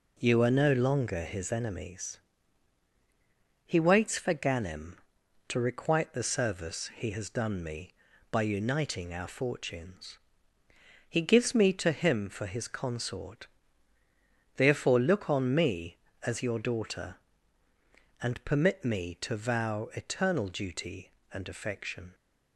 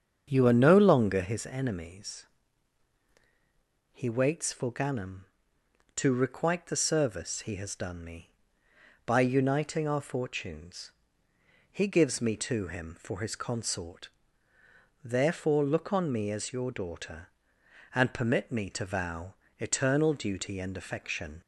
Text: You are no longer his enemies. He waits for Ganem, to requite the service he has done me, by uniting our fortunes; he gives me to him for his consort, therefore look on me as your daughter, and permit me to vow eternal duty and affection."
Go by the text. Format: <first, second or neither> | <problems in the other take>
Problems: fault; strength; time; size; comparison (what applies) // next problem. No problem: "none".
first | starts louder than the rest; strong; until 1.4 s; 7.5 dB // pauses between "vow" and "eternal"; slight; at 19.3 s; 0.26 s long